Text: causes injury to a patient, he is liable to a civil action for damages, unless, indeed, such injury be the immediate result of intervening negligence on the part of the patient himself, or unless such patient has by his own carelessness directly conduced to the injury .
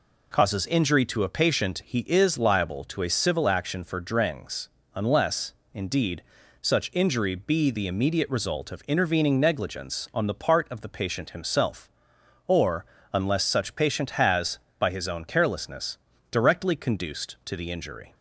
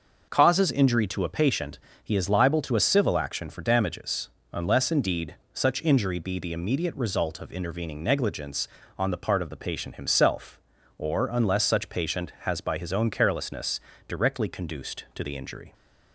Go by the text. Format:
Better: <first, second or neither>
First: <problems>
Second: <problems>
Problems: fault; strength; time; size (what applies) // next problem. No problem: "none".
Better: second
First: says "drengs" for "damages"; at 4.0 s // pauses between "or" and "unless"; slight; at 12.8 s; 0.27 s long // pauses between "carelessness" and "directly"; slight; at 15.9 s; 0.34 s long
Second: pauses between "carelessness" and "directly"; slight; at 13.7 s; 0.28 s long